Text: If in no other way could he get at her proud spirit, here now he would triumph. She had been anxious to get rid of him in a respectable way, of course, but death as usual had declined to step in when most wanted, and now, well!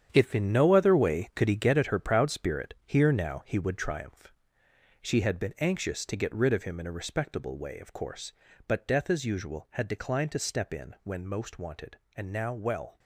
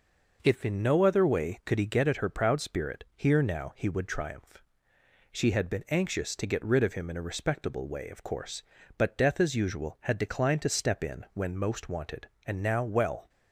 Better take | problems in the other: second | gets quieter; strong; throughout; 10 dB

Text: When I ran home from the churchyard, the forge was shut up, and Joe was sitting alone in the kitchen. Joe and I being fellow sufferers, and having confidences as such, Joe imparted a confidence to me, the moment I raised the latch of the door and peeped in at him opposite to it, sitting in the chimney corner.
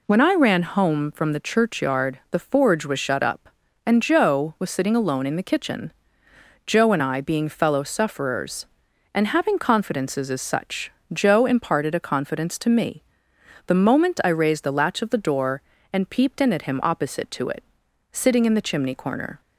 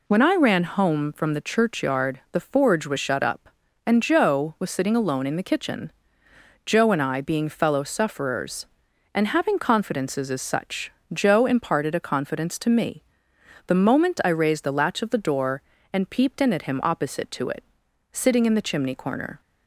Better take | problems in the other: neither | none

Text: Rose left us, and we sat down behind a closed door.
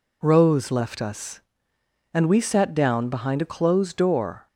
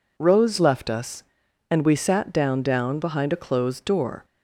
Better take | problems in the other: first | says "down" twice; at 2.6 s

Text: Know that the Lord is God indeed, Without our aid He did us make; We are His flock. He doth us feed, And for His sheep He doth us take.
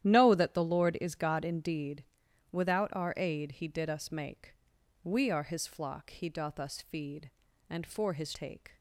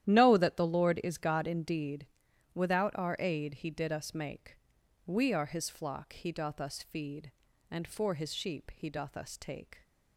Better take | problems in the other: second | starts louder than the rest; strong; until 1.0 s; 11.5 dB; strong in the second // skips "sheep He doth us"; at 8.3 s

